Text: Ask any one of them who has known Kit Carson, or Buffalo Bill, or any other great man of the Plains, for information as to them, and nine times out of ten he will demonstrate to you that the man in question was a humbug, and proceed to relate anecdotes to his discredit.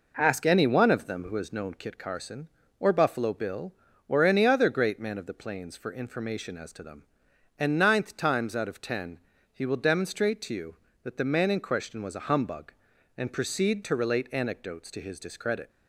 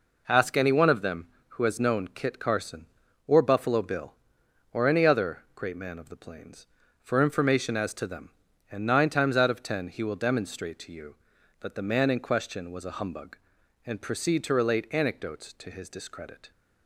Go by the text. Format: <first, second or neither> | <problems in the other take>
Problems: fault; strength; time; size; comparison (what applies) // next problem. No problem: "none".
second | says "ninth" for "nine"; at 7.7 s // pauses between "ten" and "he"; slight; at 9.1 s; 0.32 s long